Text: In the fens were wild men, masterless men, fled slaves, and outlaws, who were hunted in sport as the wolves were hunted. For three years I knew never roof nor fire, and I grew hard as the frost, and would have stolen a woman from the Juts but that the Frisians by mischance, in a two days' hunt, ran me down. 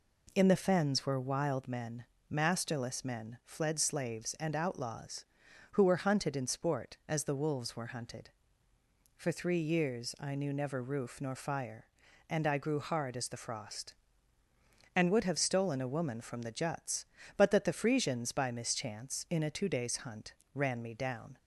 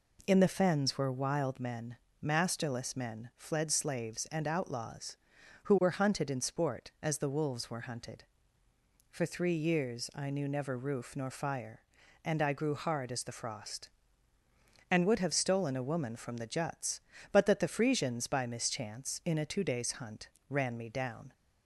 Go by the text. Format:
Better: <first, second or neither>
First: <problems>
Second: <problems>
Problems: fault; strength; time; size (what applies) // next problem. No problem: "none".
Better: neither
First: none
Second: none